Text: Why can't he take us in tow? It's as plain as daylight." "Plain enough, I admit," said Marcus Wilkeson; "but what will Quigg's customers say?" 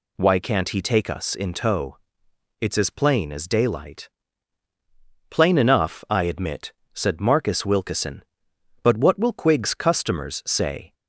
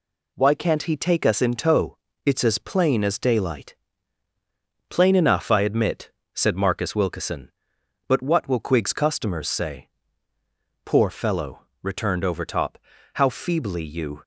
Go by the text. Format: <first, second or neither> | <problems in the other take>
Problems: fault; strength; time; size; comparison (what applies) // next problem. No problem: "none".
first | goes on to say "Poor fellow returned Overtop How feebly you"; strong; from 10.8 s on; 3.3 s long